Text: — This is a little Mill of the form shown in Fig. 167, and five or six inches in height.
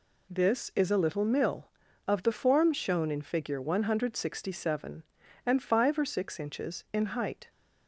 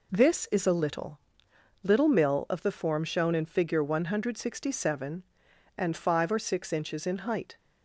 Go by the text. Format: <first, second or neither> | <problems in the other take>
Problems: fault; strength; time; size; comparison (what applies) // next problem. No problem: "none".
first | says "little" twice; at 1.8 s